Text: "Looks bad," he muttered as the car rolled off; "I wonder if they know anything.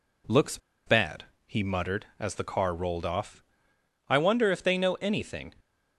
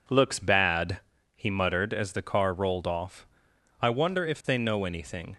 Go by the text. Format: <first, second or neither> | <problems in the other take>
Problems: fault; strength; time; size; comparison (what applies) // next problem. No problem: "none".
second | pauses between "Looks" and "bad"; slight; at 0.5 s; 0.29 s long